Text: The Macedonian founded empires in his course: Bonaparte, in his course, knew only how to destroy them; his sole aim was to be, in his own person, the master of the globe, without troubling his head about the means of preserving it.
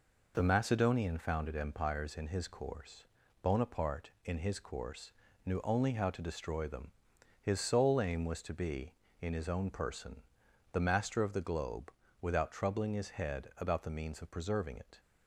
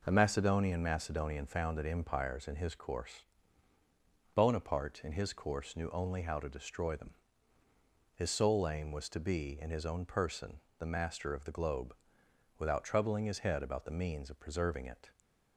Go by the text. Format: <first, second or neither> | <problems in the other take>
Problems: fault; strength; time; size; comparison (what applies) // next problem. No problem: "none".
first | says "Macedonian" twice; at 0.8 s